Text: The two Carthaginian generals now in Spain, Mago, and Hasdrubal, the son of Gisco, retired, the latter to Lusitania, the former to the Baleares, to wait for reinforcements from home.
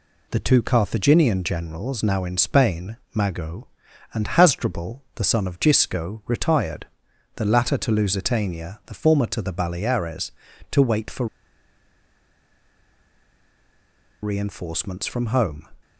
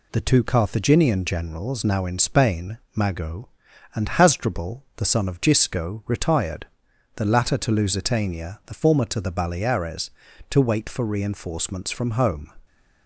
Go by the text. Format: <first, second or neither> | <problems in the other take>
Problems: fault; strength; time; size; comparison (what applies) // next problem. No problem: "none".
second | pauses between "for" and "reinforcements"; strong; at 11.2 s; 2.9 s long